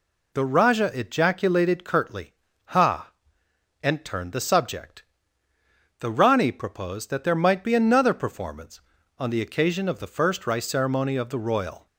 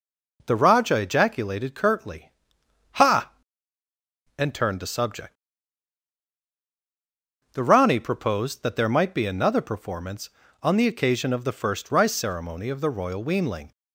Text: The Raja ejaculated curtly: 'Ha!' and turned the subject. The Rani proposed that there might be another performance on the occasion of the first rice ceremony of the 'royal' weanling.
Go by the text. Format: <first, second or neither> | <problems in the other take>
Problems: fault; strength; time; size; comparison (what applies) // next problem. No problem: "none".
second | stops before "weanling"; at 11.8 s